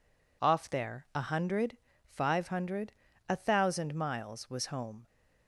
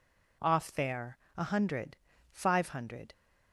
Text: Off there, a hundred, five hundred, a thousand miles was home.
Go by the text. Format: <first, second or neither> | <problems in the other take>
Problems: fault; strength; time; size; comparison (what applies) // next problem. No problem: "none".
first | stops before "a thousand miles was home"; at 3.1 s